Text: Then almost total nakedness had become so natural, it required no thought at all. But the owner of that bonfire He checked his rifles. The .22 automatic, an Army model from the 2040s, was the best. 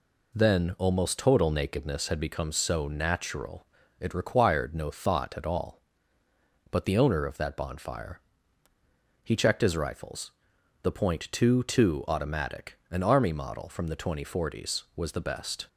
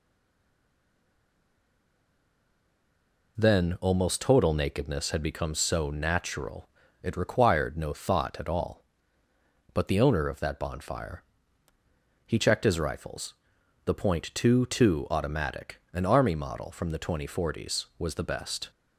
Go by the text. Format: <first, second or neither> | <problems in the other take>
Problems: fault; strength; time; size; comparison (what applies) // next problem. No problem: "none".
first | stays silent before the first word; strong; until 3.3 s; 3.3 s long // pauses between "bonfire" and "He"; at 11.2 s; 1.0 s long; also in the first